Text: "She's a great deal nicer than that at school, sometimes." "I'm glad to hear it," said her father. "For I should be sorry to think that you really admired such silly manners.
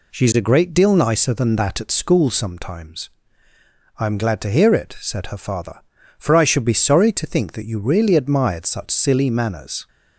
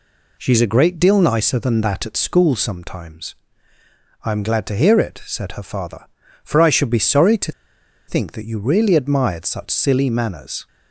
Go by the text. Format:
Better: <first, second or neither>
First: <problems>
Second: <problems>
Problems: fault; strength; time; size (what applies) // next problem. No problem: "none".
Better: first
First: none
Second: pauses between "to" and "think"; noticeable; at 7.5 s; 0.57 s long